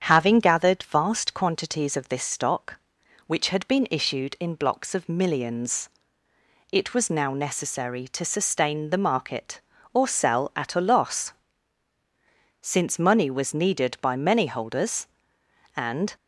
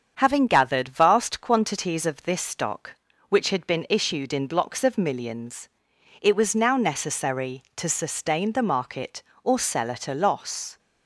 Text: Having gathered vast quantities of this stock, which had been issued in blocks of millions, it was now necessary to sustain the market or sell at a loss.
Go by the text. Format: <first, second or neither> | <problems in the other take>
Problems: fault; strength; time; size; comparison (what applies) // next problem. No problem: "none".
second | starts louder than the rest; strong; until 1.0 s; 8.5 dB; strong in the second // goes on to say "Since money was needed by many holders and"; strong; from 12.6 s on; 3.5 s long